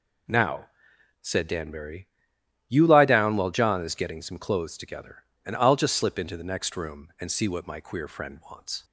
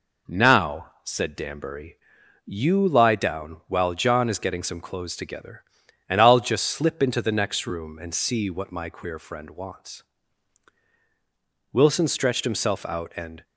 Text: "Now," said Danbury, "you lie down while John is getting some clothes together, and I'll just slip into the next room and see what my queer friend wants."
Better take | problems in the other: first | goes on to say "Wilson stretched himself out and"; strong; from 11.7 s on; 1.7 s long

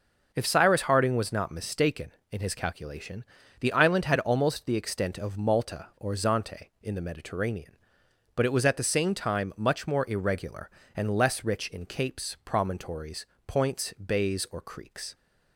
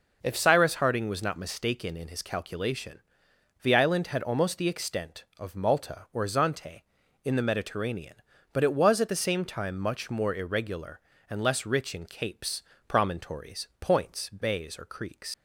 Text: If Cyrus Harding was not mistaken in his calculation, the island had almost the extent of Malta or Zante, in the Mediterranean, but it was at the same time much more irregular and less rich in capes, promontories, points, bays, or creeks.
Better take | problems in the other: first | leaves "creeks" unfinished; at 15.3 s; 75 ms

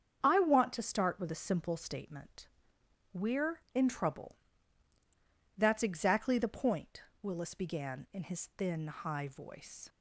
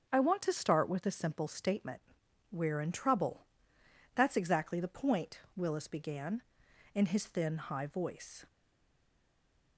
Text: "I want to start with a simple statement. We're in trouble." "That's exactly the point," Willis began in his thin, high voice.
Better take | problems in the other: first | starts louder than the rest; strong; until 1.1 s; 7 dB; strong in the first // stays silent after the last word; noticeable; from 8.4 s on; 1.3 s long

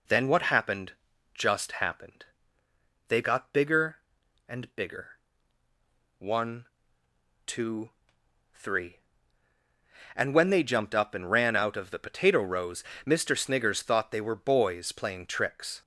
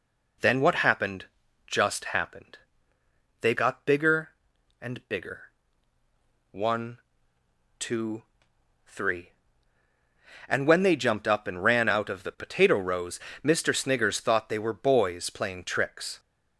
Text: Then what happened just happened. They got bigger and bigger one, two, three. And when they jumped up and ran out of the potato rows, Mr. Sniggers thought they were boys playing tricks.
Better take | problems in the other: neither | pauses between "happened" and "just"; the same in both // pauses between "bigger" and "one"; the same in both

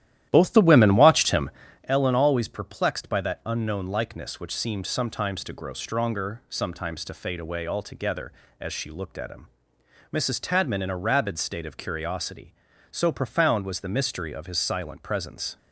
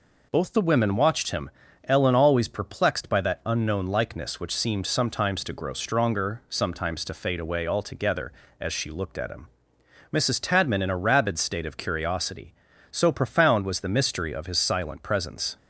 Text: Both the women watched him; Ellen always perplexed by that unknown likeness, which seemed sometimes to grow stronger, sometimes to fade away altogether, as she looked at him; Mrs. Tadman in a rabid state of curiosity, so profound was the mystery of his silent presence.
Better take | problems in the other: second | starts louder than the rest; strong; until 1.9 s; 12.5 dB

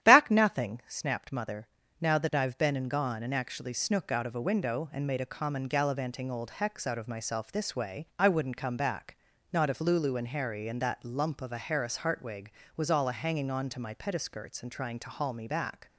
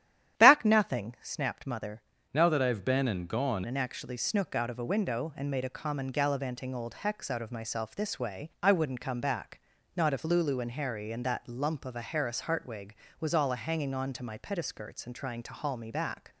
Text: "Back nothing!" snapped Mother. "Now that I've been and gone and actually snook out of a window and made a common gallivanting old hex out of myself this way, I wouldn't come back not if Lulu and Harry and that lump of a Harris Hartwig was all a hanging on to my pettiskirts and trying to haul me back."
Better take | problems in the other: first | starts louder than the rest; strong; until 1.4 s; 11 dB; strong in the first // changes voice from "Now" to "gone"; from 2.3 to 3.6 s; 1.3 s long // pauses between "back" and "not"; slight; at 9.5 s; 0.34 s long; slight in the first

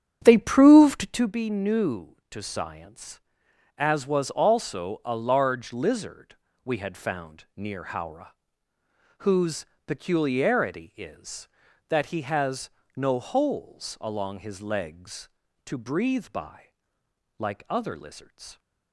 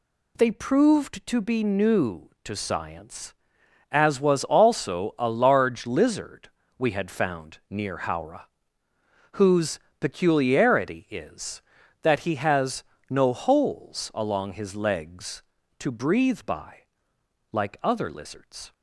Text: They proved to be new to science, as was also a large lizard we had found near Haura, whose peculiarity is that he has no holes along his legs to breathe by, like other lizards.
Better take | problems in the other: second | starts louder than the rest; strong; until 1.4 s; 8.5 dB // pauses between "lizard" and "we"; slight; at 6.3 s; 0.28 s long; slight in the second // pauses between "whose" and "peculiarity"; slight; at 9.6 s; 0.22 s long; slight in the second // pauses between "has" and "no"; slight; at 12.7 s; 0.24 s long; slight in the second

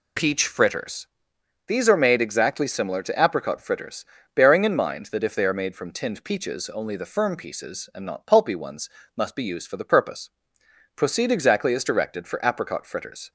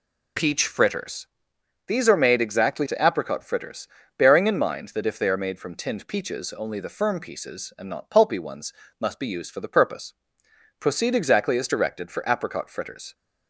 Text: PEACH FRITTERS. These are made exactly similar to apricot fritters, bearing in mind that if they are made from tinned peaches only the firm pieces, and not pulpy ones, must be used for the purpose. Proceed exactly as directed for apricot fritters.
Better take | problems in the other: first | skips "similar"; at 2.8 s

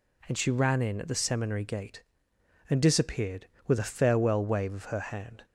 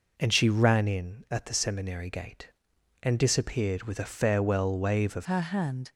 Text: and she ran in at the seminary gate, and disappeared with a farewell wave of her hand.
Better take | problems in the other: first | changes voice at "her"; from 5.2 s on; 0.6 s long

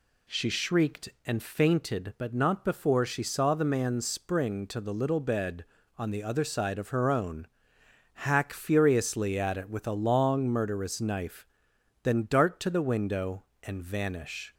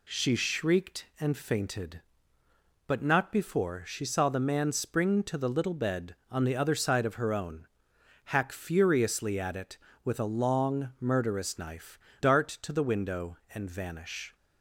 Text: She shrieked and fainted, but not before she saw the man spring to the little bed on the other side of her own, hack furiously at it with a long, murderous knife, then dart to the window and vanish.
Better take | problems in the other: first | skips "then"; at 12.1 s

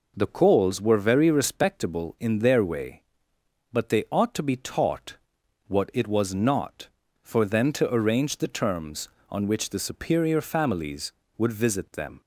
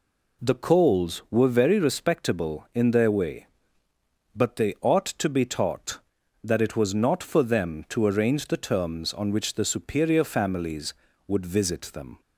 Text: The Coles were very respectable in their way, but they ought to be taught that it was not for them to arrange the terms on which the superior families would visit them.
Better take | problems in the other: second | says "what" for "that"; at 5.6 s

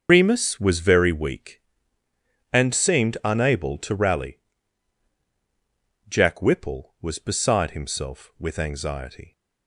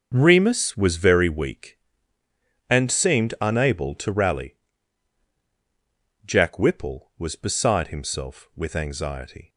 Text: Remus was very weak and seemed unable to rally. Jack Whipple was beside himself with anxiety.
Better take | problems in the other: second | loses the start of "Remus"; at 0.0 s; 150 ms // starts louder than the rest; until 1.1 s; 6.5 dB; noticeable in the second

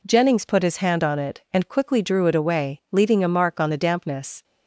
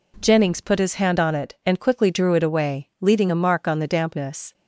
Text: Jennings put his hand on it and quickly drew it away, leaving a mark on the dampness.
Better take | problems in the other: neither | none

